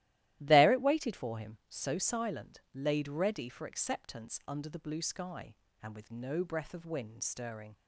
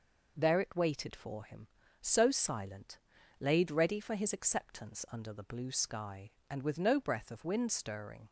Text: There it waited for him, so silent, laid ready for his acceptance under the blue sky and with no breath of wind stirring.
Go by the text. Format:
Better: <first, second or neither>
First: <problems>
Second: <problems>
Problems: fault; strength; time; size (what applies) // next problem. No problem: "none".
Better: second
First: starts louder than the rest; strong; until 1.4 s; 15 dB // skips "his"; at 3.6 s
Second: none